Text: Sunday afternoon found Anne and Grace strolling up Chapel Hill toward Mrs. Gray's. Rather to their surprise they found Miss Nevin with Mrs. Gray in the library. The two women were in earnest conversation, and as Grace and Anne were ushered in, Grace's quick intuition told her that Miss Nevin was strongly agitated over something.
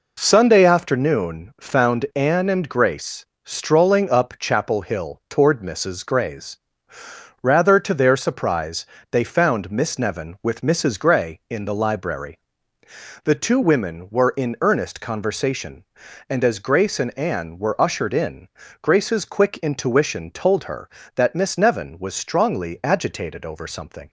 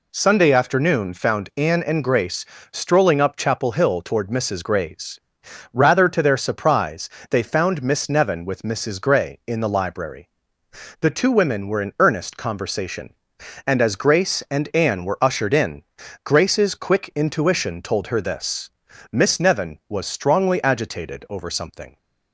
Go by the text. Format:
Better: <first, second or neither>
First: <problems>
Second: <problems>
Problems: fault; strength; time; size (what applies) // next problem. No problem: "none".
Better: first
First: pauses between "Grace" and "strolling"; slight; at 3.2 s; 0.20 s long // pauses between "surprise" and "they"; slight; at 8.8 s; 0.28 s long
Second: pauses between "Grace" and "strolling"; slight; at 2.4 s; 0.28 s long // pauses between "surprise" and "they"; slight; at 7.0 s; 0.20 s long // says "this" for "that"; at 18.2 s